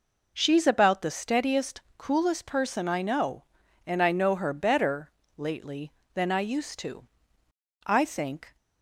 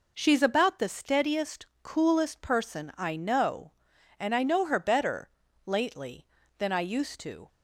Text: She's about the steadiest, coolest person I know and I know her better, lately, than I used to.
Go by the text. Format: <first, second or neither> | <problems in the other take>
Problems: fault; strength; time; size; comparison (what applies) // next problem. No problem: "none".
second | goes on to say "I think"; noticeable; from 7.8 s on; 0.70 s long